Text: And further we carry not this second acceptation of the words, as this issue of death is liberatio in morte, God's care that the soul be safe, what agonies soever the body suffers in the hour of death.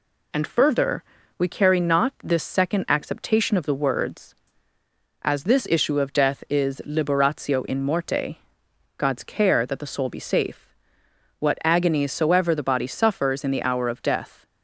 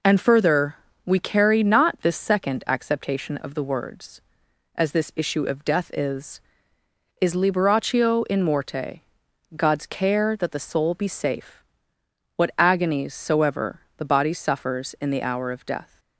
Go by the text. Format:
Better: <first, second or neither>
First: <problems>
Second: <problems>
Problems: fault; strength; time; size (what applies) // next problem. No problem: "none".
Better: first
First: pauses between "further" and "we"; slight; at 1.0 s; 0.34 s long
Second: pauses between "further" and "we"; slight; at 0.7 s; 0.30 s long // says "is" twice; at 7.1 s // pauses between "soever" and "the"; slight; at 13.8 s; 0.16 s long